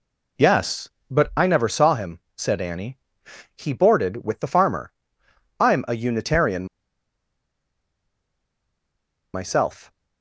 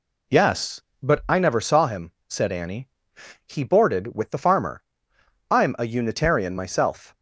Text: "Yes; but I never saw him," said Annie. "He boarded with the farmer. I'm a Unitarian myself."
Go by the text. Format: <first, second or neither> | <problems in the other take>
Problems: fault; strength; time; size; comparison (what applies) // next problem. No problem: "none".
second | pauses between "Unitarian" and "myself"; strong; at 6.6 s; 2.6 s long